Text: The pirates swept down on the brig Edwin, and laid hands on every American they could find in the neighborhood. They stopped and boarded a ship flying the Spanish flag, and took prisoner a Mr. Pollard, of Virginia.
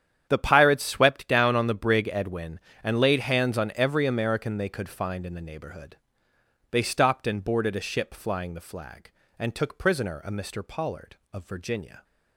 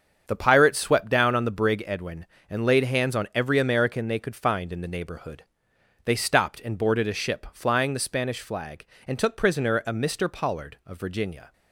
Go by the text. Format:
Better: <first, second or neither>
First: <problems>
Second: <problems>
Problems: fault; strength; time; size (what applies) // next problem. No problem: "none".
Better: second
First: starts louder than the rest; strong; until 1.3 s; 9 dB // skips "Spanish"; at 8.5 s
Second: starts louder than the rest; strong; until 1.2 s; 7 dB